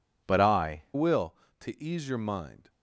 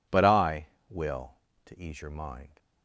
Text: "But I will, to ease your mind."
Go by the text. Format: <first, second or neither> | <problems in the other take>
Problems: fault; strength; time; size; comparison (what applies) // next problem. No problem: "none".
second | changes voice at "will"; from 0.9 s on; 1.7 s long